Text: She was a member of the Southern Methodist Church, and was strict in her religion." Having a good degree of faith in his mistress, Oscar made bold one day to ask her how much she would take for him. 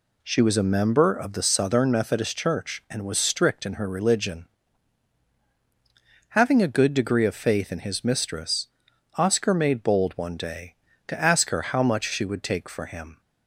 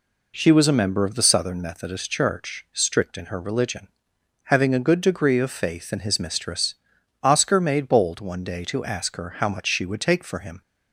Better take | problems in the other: first | skips "and was"; at 2.6 s

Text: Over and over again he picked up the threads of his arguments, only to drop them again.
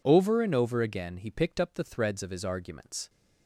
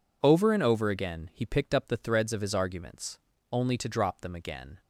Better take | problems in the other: second | stops before "only to drop them again"; at 3.0 s

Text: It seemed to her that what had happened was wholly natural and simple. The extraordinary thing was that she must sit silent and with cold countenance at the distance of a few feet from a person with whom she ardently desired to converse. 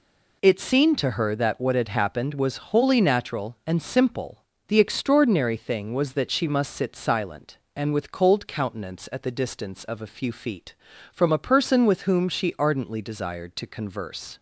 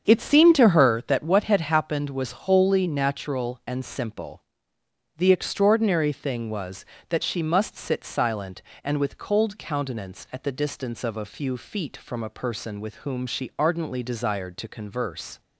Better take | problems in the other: first | starts louder than the rest; strong; until 1.2 s; 7.5 dB

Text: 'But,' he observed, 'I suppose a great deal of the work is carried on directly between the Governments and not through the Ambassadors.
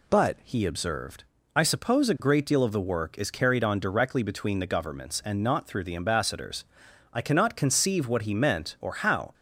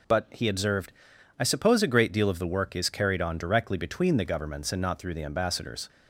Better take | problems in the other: second | goes on to say "I cannot conceive what he meant or how"; strong; from 7.1 s on; 2.2 s long

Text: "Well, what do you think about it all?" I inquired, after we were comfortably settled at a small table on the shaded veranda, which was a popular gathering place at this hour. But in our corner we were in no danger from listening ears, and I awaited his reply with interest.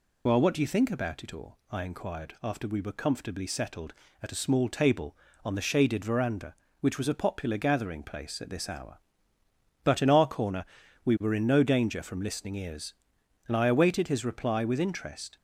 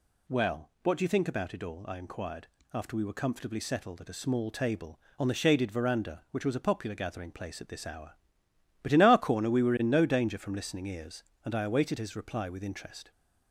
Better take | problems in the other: second | loses the start of "Well"; at 0.2 s; 40 ms // pauses between "corner" and "we"; at 10.6 s; 0.38 s long

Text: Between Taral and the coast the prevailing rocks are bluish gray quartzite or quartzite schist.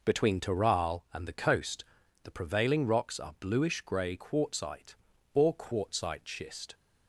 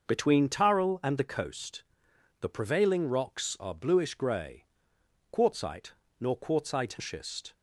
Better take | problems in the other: first | pauses between "coast" and "the"; noticeable; at 1.8 s; 0.58 s long; also in the first // pauses between "gray" and "quartzite"; noticeable; at 4.6 s; 0.66 s long // says "nor" for "or"; at 6.1 s

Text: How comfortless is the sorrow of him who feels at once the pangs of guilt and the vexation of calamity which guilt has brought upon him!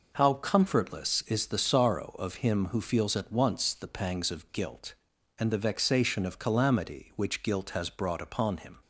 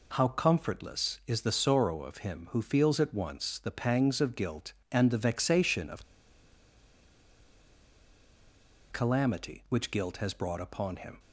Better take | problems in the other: first | pauses between "of" and "calamity"; strong; at 6.0 s; 2.8 s long

